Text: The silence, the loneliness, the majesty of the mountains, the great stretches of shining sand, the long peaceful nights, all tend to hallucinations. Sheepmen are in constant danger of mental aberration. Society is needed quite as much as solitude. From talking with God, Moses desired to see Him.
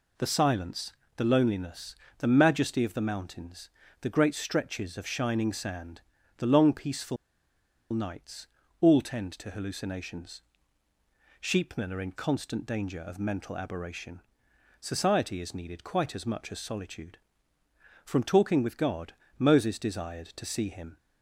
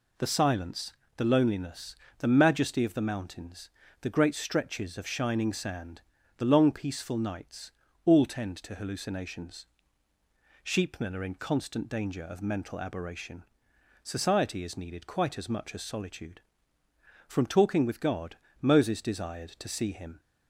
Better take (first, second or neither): second